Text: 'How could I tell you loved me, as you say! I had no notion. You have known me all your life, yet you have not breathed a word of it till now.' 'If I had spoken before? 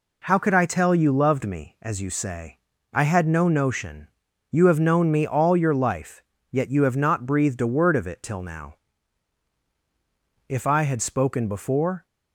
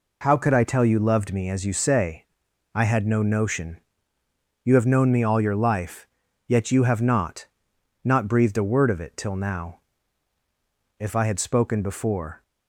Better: first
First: none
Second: says "not" twice; at 8.0 s

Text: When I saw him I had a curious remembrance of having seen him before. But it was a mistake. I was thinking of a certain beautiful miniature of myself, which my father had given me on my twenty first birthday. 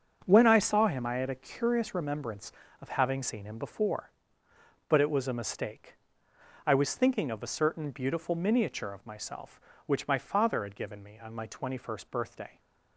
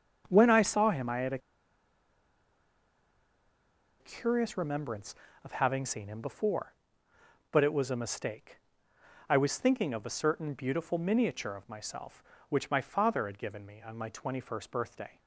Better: first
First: starts louder than the rest; strong; until 1.2 s; 7 dB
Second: starts louder than the rest; strong; until 1.2 s; 7 dB // pauses between "a" and "curious"; strong; at 1.3 s; 2.6 s long

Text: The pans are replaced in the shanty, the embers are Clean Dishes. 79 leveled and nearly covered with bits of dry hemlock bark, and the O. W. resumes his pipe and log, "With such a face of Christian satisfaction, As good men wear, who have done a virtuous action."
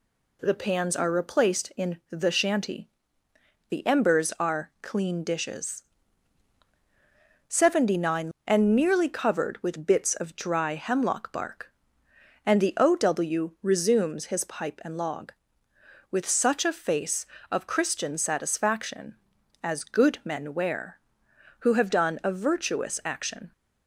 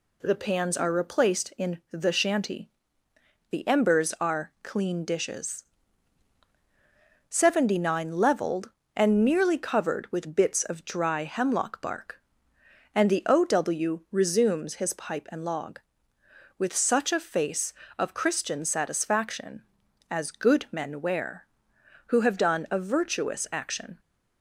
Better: second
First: skips "leveled"; at 8.3 s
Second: none

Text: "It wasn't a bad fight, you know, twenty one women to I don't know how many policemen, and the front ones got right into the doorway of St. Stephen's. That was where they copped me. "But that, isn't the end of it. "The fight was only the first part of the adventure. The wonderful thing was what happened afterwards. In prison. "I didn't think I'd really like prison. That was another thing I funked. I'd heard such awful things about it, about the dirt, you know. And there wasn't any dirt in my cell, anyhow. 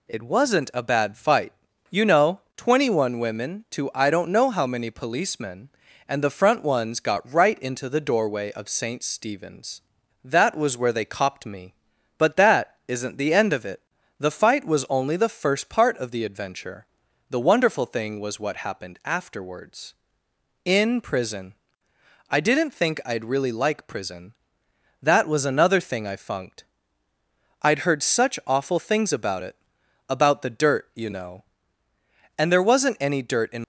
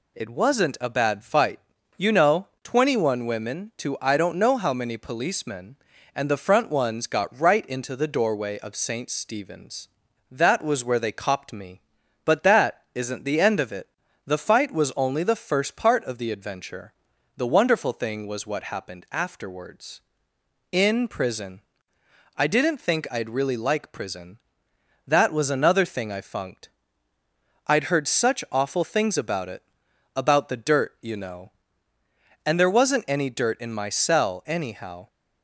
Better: second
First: stops before "my cell anyhow"; at 33.6 s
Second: none

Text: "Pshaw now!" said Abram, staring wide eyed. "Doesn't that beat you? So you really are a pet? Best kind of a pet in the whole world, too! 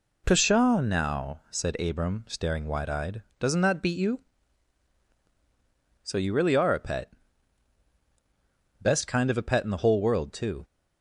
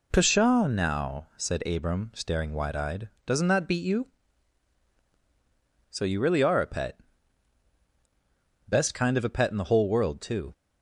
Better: neither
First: none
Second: none

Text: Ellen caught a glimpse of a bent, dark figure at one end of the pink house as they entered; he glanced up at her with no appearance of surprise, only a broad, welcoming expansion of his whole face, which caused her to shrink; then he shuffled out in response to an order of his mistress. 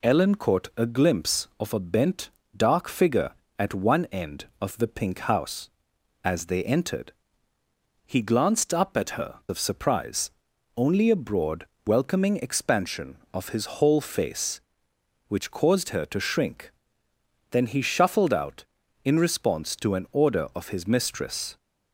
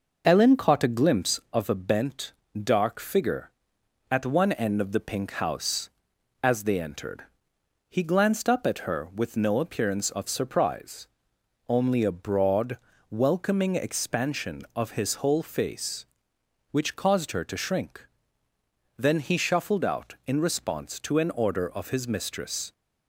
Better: second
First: skips "with no appearance"; at 9.4 s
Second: none

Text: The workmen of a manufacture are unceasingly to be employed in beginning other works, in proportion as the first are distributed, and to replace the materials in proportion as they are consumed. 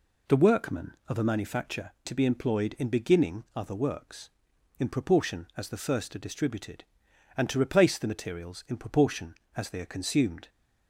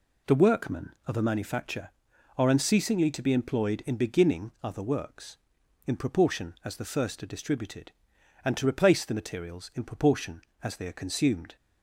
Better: second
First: skips "are unceasingly"; at 1.9 s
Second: none

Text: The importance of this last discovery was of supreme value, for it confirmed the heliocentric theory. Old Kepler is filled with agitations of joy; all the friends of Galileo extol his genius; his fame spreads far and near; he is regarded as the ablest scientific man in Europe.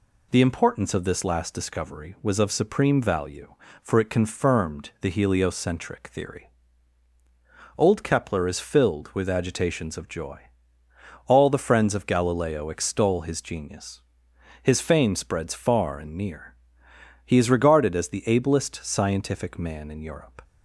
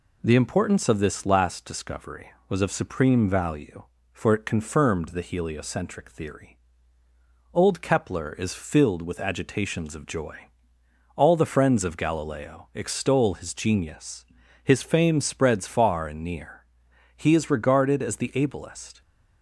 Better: first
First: none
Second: stops before "scientific man in Europe"; at 19.0 s

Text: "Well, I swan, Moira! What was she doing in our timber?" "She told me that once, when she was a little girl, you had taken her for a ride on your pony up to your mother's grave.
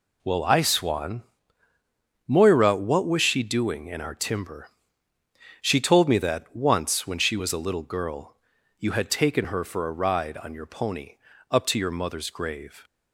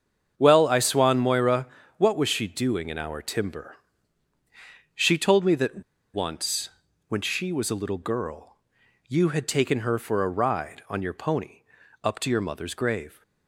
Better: first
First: pauses between "pony" and "up"; slight; at 11.1 s; 0.34 s long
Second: starts louder than the rest; strong; until 1.3 s; 7.5 dB // pauses between "that" and "once"; slight; at 5.8 s; 0.31 s long // pauses between "pony" and "up"; at 11.6 s; 0.40 s long

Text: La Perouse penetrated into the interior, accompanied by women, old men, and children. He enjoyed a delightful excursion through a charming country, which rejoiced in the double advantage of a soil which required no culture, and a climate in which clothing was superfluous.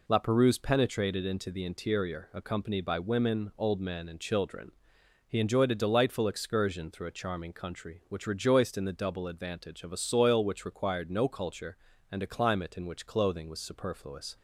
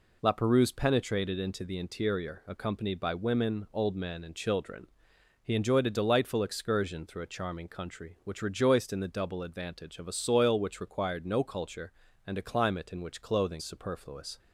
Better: first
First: none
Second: skips "was"; at 13.6 s

